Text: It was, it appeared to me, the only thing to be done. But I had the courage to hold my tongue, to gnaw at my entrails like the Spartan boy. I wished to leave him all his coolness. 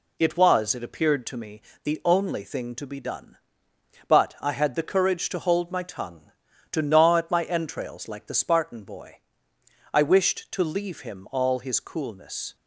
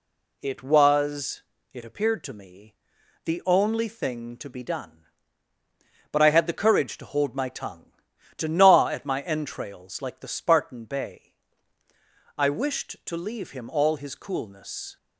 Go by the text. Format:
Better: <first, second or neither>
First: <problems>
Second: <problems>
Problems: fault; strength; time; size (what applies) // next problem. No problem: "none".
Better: first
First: none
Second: says "bay" for "boy"; at 10.8 s